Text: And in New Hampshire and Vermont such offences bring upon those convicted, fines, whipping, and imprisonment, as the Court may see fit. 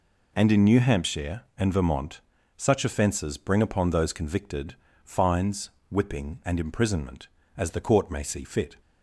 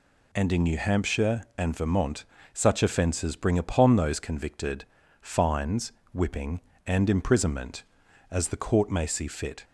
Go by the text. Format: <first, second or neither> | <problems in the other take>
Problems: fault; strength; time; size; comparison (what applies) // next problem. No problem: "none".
neither | pauses between "Vermont" and "such"; slight; the same in both